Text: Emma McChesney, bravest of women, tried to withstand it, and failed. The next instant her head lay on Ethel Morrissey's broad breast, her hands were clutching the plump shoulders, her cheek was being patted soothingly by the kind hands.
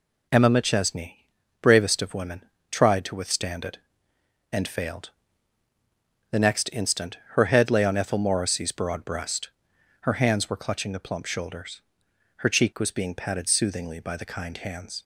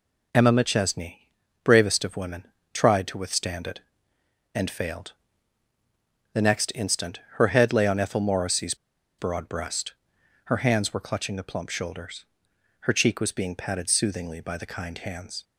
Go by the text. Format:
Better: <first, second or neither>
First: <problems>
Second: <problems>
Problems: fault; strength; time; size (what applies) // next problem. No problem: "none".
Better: first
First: none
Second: pauses between "Morrissey's" and "broad"; at 8.7 s; 0.44 s long